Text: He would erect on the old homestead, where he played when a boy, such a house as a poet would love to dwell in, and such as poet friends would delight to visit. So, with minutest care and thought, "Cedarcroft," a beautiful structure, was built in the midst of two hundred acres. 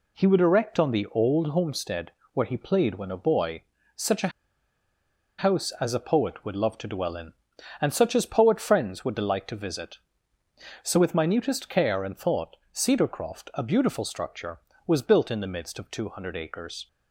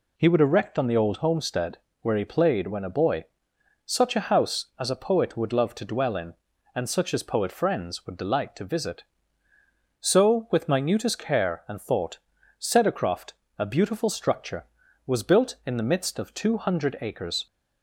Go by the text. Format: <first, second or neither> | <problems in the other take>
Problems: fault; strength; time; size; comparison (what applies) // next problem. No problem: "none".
second | pauses between "a" and "house"; at 4.3 s; 1.0 s long